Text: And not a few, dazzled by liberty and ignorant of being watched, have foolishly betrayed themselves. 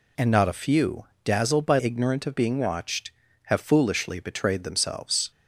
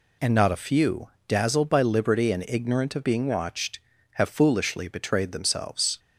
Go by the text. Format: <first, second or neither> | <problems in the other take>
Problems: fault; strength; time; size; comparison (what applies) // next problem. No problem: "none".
second | skips "liberty and"; at 1.7 s